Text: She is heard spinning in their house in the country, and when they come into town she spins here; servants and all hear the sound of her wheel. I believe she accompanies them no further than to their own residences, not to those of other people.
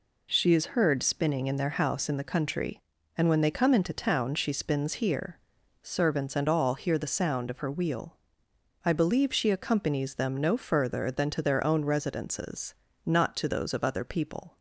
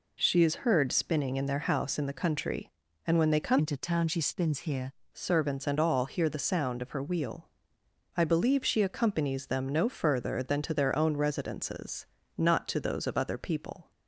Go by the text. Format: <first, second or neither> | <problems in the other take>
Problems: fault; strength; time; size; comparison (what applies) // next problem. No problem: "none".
first | changes voice from "into" to "here"; from 3.5 to 4.9 s; 1.4 s long